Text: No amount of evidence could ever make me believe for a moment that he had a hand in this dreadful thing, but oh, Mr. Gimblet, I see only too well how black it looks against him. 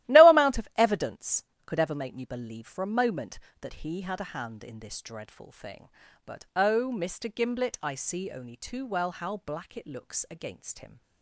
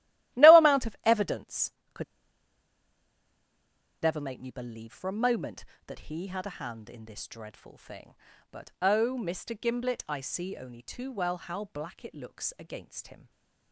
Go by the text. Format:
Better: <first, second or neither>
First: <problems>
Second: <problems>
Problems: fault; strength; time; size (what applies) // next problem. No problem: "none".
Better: first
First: starts louder than the rest; strong; until 1.1 s; 15 dB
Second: starts louder than the rest; strong; until 1.4 s; 15 dB // pauses between "could" and "ever"; strong; at 2.0 s; 1.9 s long